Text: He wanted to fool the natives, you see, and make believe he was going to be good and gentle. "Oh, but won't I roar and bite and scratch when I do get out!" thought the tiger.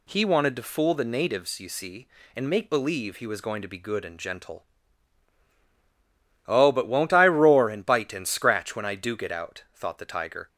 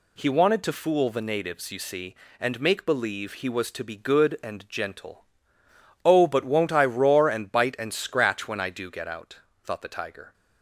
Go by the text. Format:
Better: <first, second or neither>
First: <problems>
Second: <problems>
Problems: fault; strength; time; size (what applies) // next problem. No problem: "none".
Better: first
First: none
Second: skips "going"; at 3.6 s